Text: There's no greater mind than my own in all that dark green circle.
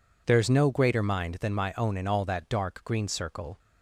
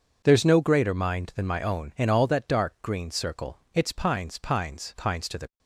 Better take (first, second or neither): first